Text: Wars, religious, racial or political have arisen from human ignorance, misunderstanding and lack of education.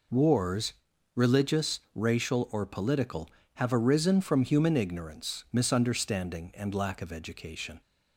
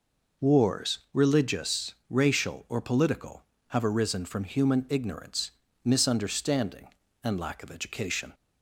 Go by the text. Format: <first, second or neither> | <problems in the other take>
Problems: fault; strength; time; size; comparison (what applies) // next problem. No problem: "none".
neither | none